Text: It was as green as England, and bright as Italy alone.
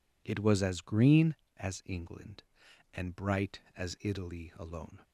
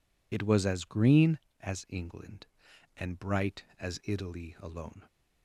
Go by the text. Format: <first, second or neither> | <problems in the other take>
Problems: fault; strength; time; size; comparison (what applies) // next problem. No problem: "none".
first | loses the start of "It"; at 0.3 s; 35 ms